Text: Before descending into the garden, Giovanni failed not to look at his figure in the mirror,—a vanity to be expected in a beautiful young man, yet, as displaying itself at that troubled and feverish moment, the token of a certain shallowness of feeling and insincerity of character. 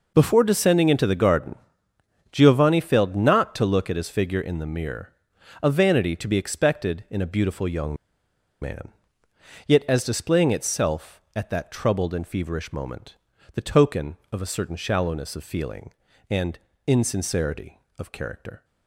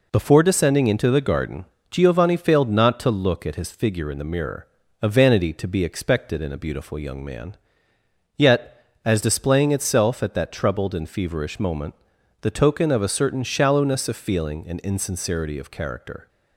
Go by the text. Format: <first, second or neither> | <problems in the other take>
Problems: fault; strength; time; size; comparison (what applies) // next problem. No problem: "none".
second | pauses between "young" and "man"; noticeable; at 7.9 s; 0.66 s long // pauses between "and" and "insincerity"; slight; at 16.5 s; 0.30 s long